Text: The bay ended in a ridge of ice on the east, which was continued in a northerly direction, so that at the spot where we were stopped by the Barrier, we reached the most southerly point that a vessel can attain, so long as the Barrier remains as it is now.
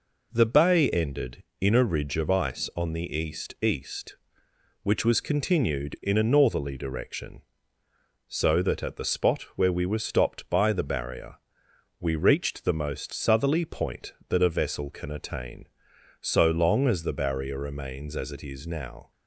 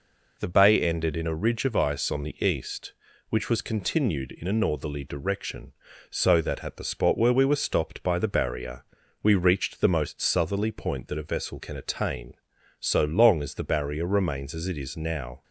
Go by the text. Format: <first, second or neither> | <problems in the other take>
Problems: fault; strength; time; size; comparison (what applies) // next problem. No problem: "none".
second | says "east" twice; at 3.6 s